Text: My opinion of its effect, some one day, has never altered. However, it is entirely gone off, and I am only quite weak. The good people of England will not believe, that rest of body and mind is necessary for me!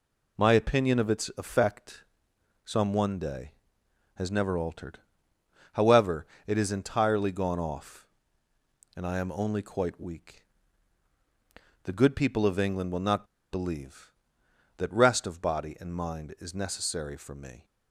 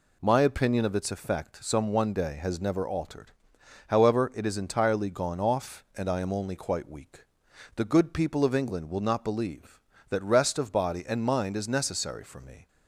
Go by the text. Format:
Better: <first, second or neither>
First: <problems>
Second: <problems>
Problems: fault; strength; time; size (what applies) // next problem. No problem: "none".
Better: second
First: pauses between "not" and "believe"; slight; at 13.2 s; 0.26 s long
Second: none